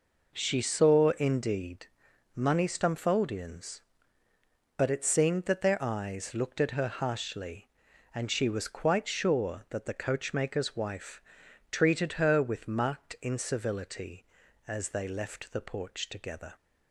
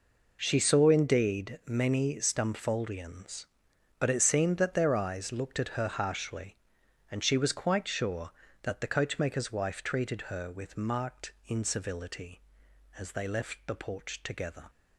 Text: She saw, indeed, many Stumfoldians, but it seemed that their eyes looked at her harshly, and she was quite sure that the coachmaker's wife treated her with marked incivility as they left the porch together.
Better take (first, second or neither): second